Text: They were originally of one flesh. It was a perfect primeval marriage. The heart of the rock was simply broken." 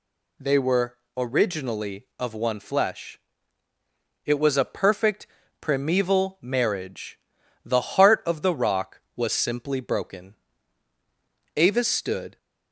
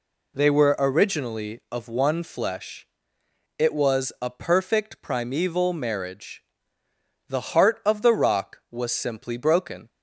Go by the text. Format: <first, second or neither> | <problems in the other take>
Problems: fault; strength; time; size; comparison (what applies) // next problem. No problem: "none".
second | pauses between "were" and "originally"; slight; at 0.9 s; 0.20 s long // pauses between "perfect" and "primeval"; slight; at 5.2 s; 0.36 s long // goes on to say "Avis stood"; noticeable; from 11.5 s on; 0.82 s long